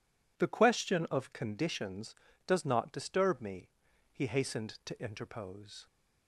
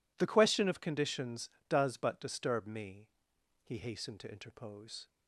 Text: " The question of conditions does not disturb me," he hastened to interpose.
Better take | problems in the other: first | says "but" for "not"; at 1.9 s

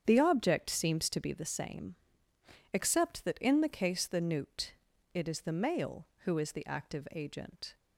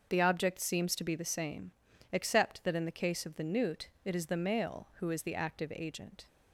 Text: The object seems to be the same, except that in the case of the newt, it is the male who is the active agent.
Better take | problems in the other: second | starts louder than the rest; strong; until 1.0 s; 8 dB; also in the second // skips "of"; at 4.0 s

